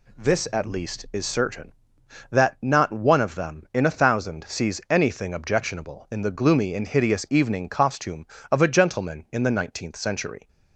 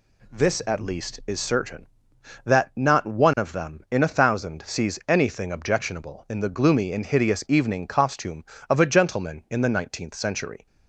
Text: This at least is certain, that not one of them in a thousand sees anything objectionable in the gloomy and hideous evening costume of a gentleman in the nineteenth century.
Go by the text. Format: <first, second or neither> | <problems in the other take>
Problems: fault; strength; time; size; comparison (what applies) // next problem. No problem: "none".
neither | none